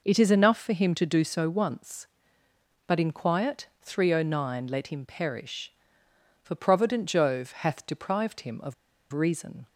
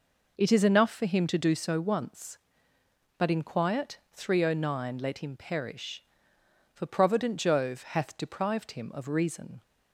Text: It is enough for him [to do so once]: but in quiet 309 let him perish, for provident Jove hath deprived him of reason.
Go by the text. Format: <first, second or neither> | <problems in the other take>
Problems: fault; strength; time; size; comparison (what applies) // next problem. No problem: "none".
second | pauses between "of" and "reason"; at 8.7 s; 0.38 s long